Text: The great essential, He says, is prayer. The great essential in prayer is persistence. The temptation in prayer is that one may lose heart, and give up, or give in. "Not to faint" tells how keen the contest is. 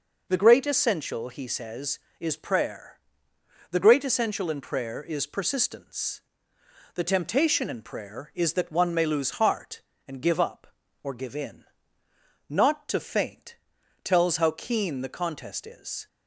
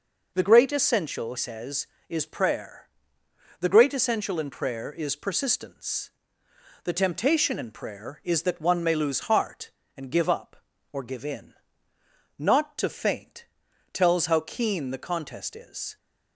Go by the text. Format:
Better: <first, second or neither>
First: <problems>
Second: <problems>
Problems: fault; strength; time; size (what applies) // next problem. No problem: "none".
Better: first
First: pauses between "faint" and "tells"; noticeable; at 13.5 s; 0.46 s long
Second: skips "He"; at 1.3 s // pauses between "faint" and "tells"; noticeable; at 13.4 s; 0.46 s long